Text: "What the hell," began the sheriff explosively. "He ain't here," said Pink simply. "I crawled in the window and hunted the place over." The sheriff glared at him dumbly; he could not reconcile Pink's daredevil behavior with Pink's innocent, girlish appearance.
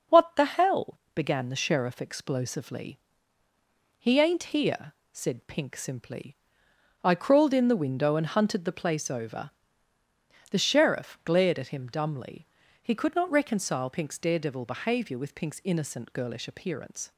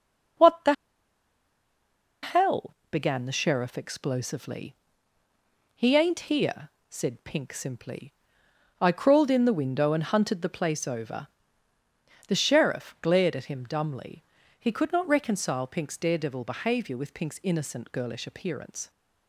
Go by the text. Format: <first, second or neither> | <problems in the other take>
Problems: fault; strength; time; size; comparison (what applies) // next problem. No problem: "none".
first | starts louder than the rest; noticeable; until 3.0 s; 6 dB; noticeable in the first // pauses between "the" and "hell"; strong; at 0.7 s; 1.5 s long